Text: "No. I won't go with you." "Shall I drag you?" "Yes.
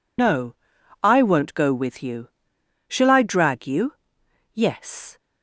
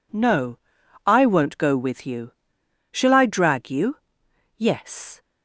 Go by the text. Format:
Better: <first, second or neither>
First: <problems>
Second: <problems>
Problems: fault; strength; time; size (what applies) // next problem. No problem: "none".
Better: second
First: loses the start of "No"; at 0.1 s; 110 ms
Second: none